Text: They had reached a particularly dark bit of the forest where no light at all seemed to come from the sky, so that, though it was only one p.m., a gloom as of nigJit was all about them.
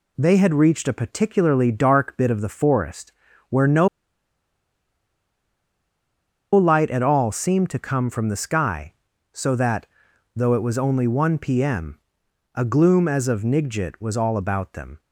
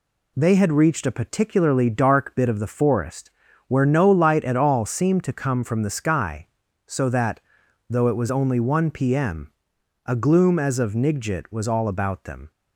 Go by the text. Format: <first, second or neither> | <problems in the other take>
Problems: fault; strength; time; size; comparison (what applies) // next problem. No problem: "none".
second | pauses between "forest" and "where"; at 3.1 s; 0.38 s long; also in the second // pauses between "no" and "light"; strong; at 3.8 s; 2.6 s long